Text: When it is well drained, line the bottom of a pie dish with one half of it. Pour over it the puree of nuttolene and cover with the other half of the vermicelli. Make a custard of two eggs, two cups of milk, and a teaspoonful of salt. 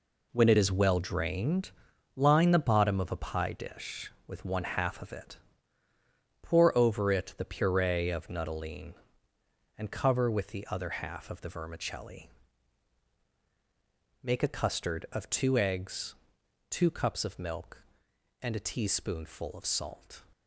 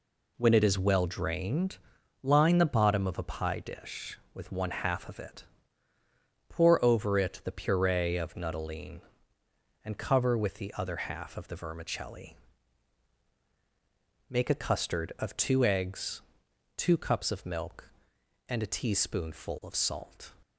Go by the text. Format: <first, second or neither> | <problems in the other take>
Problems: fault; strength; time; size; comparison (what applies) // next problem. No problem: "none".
second | gets quieter; strong; throughout; 8.5 dB